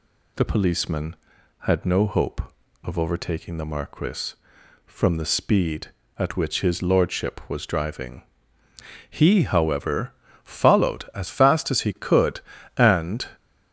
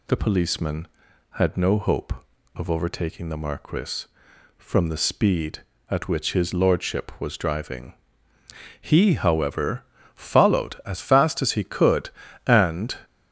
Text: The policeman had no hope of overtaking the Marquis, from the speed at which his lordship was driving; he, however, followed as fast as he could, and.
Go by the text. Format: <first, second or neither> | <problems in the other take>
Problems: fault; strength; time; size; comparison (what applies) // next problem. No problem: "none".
neither | none